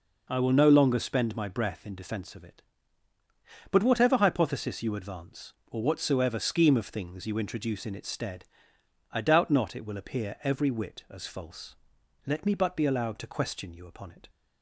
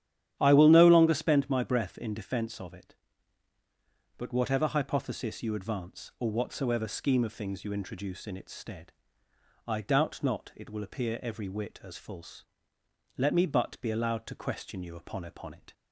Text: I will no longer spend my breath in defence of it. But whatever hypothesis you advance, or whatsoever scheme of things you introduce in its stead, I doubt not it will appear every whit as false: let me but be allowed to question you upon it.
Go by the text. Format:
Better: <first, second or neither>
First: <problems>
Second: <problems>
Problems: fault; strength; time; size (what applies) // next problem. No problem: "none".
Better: first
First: none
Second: starts louder than the rest; strong; until 1.4 s; 11 dB // says "upon" twice; at 15.2 s